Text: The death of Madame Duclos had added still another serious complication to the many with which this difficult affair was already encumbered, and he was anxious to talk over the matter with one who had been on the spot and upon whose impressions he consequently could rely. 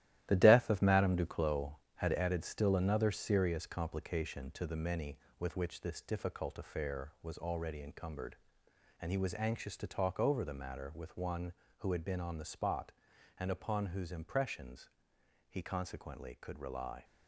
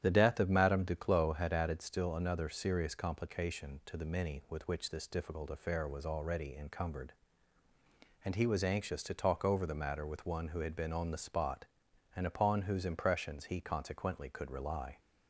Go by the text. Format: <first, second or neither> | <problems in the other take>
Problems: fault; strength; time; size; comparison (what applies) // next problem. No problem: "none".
second | gets quieter; strong; throughout; 8 dB // starts louder than the rest; strong; until 1.2 s; 13.5 dB; strong in the second // pauses between "impressions" and "he"; noticeable; at 14.8 s; 0.62 s long